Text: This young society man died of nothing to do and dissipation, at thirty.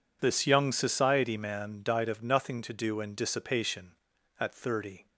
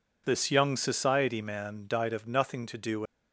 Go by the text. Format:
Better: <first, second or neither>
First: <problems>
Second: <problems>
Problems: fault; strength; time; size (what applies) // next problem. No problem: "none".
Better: first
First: none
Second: stops before "and dissipation at thirty"; at 3.0 s